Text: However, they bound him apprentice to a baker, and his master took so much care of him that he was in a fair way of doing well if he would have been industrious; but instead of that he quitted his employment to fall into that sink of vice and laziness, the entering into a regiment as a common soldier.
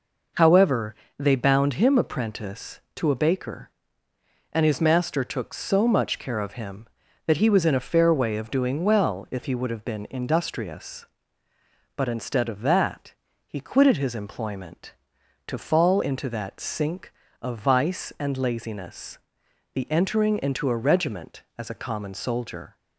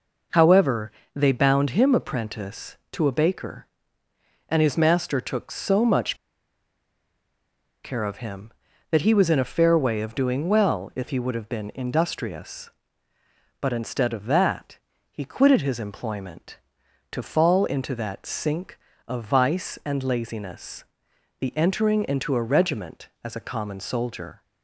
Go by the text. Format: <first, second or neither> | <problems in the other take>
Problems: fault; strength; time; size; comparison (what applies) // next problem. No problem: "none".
first | pauses between "much" and "care"; strong; at 6.1 s; 1.6 s long // pauses between "that" and "he"; slight; at 14.7 s; 0.32 s long; slight in the first